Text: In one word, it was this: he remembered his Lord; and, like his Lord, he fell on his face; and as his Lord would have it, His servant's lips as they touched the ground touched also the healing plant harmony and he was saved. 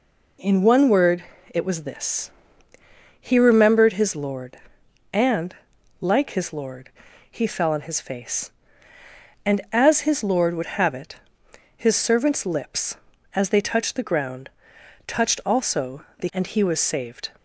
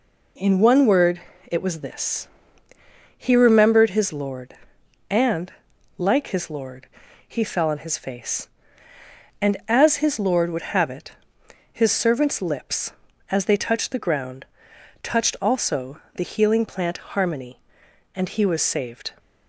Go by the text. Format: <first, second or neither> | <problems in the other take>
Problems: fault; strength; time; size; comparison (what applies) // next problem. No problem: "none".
second | pauses between "ground" and "touched"; noticeable; at 14.4 s; 0.60 s long; noticeable in the second // skips "healing plant harmony"; at 16.2 s